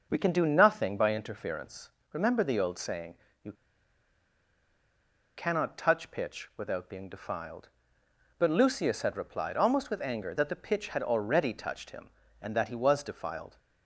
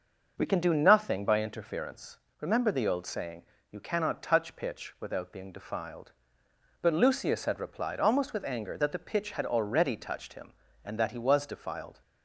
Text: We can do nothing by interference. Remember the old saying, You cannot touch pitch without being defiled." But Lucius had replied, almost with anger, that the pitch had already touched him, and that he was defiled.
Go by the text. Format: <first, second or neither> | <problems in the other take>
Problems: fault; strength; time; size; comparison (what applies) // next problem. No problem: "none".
second | starts louder than the rest; noticeable; until 1.1 s; 6 dB // pauses between "You" and "cannot"; strong; at 3.5 s; 1.8 s long